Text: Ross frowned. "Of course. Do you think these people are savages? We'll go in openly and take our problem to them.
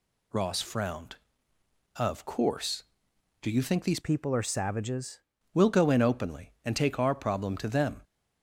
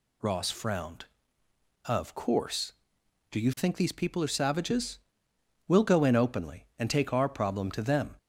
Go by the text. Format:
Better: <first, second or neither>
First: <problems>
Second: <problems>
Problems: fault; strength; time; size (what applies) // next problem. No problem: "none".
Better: second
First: changes voice from "people" to "savages"; from 4.0 to 5.2 s; 1.2 s long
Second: none